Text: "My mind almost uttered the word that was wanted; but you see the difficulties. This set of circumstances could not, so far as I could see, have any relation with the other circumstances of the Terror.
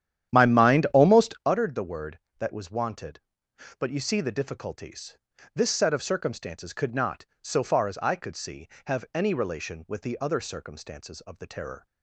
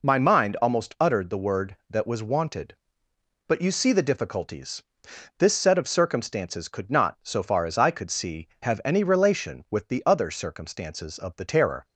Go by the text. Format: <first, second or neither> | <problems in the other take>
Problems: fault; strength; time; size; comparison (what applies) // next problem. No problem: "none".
second | starts louder than the rest; strong; until 1.6 s; 10.5 dB